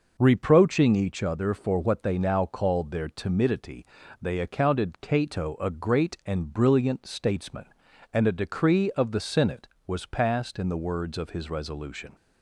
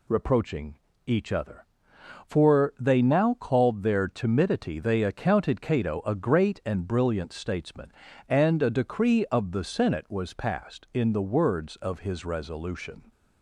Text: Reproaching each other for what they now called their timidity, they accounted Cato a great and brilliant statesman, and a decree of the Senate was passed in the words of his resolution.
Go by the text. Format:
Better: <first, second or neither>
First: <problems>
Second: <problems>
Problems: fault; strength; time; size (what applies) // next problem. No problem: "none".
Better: first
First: none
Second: pauses between "Reproaching" and "each"; slight; at 0.7 s; 0.30 s long // skips "what"; at 2.7 s